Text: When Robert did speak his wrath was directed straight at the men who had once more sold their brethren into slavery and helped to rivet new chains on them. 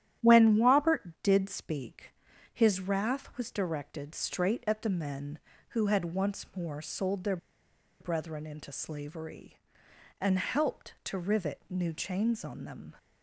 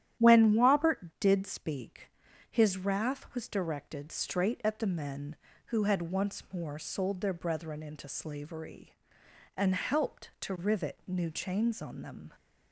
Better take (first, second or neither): second